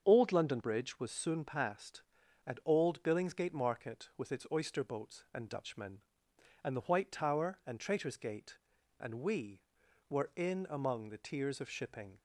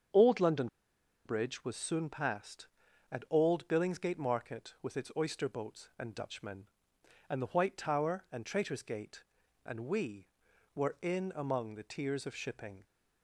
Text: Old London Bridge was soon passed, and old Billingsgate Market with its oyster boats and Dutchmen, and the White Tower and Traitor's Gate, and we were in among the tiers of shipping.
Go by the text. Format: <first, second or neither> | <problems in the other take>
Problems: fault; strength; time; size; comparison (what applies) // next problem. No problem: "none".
first | starts louder than the rest; strong; until 1.7 s; 7 dB; strong in the first // pauses between "London" and "Bridge"; noticeable; at 0.6 s; 0.58 s long